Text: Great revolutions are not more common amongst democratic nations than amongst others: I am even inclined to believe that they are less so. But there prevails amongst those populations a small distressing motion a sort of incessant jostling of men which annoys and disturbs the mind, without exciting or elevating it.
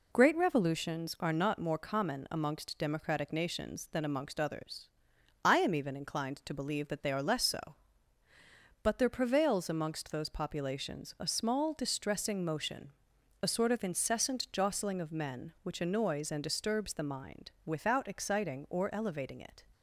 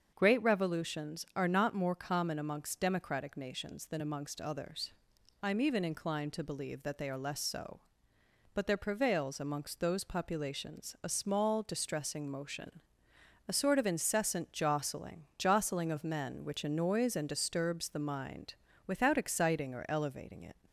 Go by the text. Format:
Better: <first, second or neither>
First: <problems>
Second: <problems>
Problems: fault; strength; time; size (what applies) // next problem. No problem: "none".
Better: first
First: pauses between "motion" and "a"; noticeable; at 12.8 s; 0.52 s long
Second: starts louder than the rest; until 1.1 s; 7 dB // pauses between "motion" and "a"; noticeable; at 12.8 s; 0.66 s long // says "jostling" twice; at 15.3 s